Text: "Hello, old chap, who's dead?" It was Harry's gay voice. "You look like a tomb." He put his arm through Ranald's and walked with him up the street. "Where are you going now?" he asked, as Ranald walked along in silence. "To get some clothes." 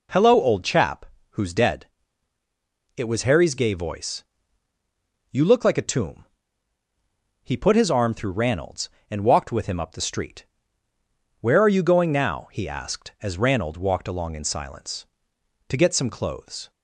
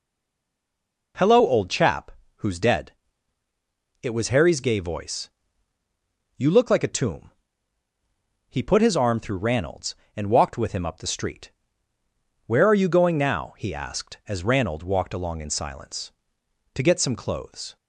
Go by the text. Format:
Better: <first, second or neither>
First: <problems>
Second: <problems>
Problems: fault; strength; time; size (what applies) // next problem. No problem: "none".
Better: first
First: none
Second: stays silent before the first word; until 1.1 s; 1.1 s long